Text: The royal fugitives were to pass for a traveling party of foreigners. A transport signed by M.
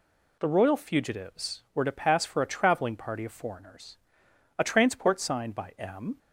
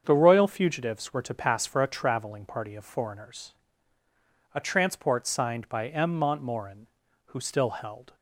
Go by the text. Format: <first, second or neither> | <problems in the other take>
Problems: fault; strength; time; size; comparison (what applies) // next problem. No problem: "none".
first | starts louder than the rest; until 1.0 s; 7 dB // goes on to say "Montmorin who still held"; strong; from 6.1 s on; 1.9 s long